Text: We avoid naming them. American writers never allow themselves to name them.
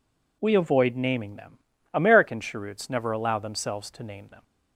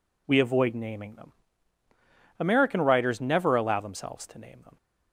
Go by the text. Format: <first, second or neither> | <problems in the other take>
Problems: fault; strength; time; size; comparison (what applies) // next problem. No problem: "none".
second | says "cheroots" for "writers"; at 2.3 s